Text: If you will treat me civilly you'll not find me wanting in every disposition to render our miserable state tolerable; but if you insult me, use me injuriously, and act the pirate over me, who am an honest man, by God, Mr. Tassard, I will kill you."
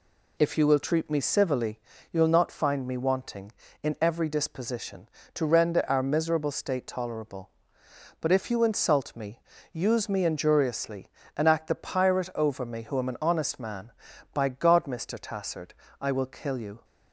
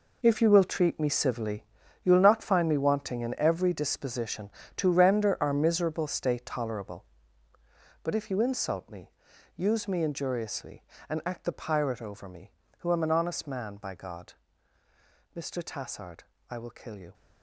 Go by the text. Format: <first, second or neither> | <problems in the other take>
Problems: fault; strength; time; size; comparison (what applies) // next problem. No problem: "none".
first | gets quieter; strong; throughout; 11.5 dB // pauses between "civilly" and "you'll"; at 1.6 s; 0.40 s long; slight in the first